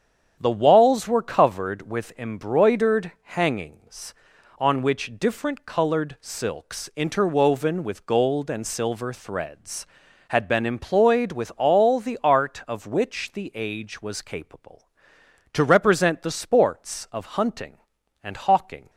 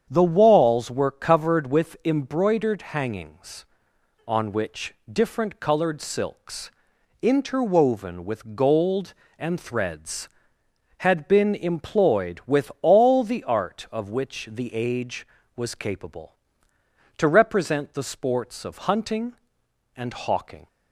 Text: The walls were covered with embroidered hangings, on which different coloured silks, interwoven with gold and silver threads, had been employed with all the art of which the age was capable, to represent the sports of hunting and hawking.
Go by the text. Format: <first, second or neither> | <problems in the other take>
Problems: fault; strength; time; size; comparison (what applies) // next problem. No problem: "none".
first | starts louder than the rest; strong; until 1.1 s; 8.5 dB; strong in the first // pauses between "which" and "different"; slight; at 4.9 s; 0.18 s long // skips "silver"; at 9.5 s